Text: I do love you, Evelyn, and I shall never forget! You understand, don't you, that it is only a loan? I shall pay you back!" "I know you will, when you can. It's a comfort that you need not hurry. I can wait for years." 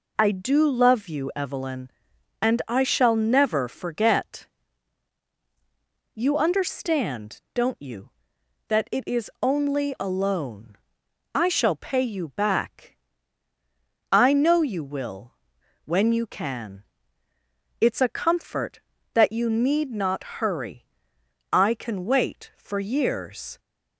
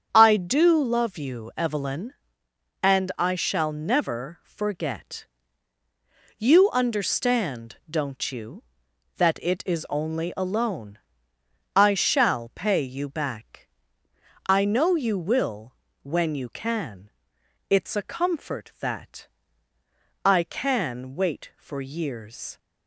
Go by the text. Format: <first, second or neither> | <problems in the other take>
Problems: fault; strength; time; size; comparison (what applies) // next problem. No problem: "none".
first | starts louder than the rest; strong; until 1.1 s; 7.5 dB // skips "you need not hurry"; at 19.7 s